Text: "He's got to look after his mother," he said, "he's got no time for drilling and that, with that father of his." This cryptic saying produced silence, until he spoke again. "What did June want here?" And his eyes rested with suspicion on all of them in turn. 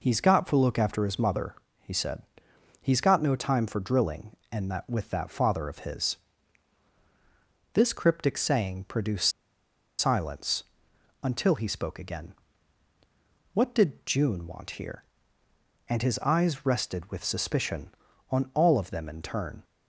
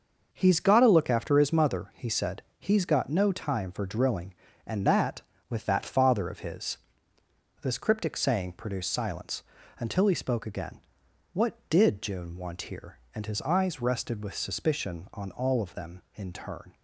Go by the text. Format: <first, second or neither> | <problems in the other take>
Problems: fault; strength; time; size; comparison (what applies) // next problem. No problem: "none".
second | pauses between "produced" and "silence"; noticeable; at 9.3 s; 0.68 s long